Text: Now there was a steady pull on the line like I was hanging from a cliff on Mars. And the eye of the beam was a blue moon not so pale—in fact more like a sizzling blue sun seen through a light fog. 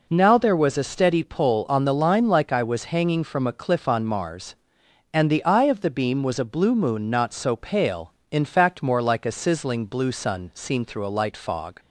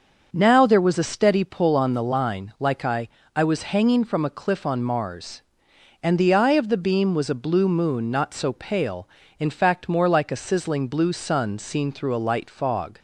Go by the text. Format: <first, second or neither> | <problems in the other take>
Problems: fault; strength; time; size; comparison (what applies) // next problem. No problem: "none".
first | starts louder than the rest; until 1.3 s; 6.5 dB // says "I" twice; at 3.3 s